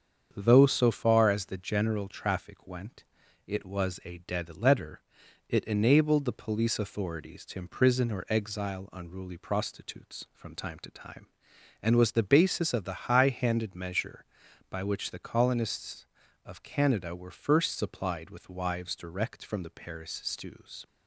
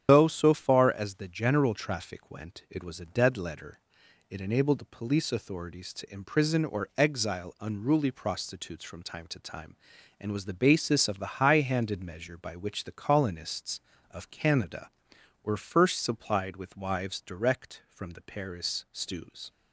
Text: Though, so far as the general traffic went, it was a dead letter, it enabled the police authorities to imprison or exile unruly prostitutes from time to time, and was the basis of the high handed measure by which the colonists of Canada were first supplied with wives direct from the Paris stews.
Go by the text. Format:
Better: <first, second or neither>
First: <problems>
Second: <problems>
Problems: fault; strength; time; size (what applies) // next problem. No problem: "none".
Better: first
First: starts louder than the rest; strong; until 1.3 s; 7.5 dB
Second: loses the start of "Though"; at 0.0 s; 100 ms // starts louder than the rest; strong; until 1.0 s; 9 dB